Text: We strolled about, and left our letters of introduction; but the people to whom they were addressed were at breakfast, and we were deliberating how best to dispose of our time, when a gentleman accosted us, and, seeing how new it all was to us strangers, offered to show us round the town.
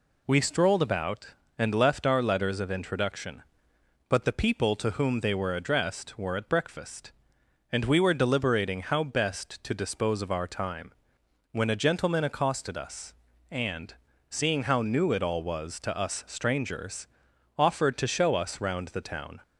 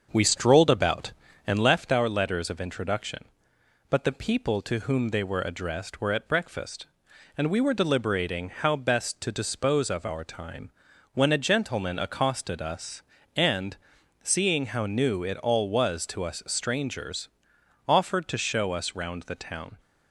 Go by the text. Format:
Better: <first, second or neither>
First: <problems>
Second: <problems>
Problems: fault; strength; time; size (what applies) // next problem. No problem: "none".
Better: first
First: none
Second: starts louder than the rest; until 1.9 s; 7 dB